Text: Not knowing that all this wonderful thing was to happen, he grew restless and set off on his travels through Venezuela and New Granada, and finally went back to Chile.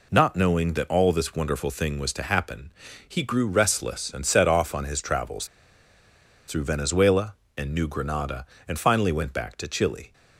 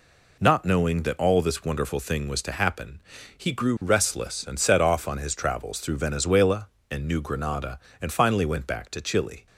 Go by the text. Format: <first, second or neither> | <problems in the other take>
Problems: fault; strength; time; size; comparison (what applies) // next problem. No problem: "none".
second | pauses between "travels" and "through"; at 5.4 s; 1.0 s long